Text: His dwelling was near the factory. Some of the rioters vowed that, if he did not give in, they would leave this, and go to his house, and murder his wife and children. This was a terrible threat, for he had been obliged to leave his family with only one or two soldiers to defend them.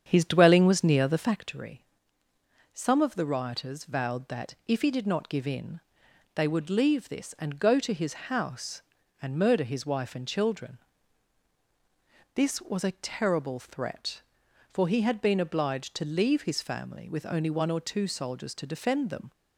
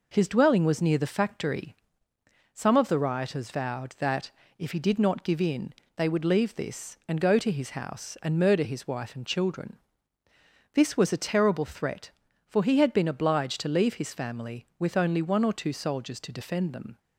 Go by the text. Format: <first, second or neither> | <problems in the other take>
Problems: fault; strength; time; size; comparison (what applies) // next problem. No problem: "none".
second | starts louder than the rest; strong; until 1.4 s; 8 dB